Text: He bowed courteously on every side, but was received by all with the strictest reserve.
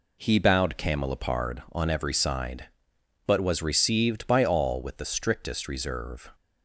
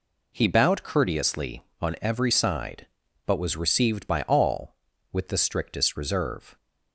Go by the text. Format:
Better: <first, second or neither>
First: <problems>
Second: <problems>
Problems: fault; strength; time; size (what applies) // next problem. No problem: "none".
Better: second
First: says "camelopard" for "courteously"; at 0.7 s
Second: none